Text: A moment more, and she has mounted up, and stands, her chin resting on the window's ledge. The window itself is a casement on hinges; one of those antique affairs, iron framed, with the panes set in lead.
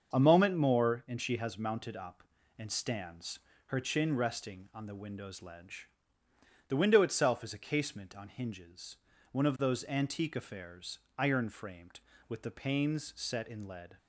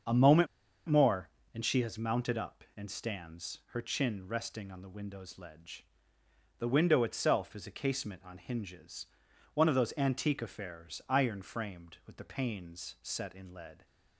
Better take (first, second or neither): first